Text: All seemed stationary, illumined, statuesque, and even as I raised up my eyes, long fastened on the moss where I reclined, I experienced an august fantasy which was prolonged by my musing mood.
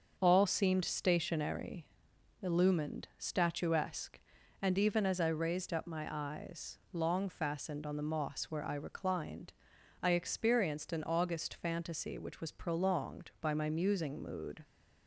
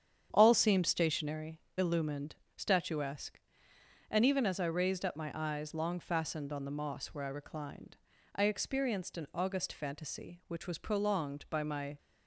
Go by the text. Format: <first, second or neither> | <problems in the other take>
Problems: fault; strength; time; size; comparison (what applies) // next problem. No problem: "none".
first | starts louder than the rest; strong; until 1.3 s; 8.5 dB; also in the first // stops before "musing mood"; at 11.9 s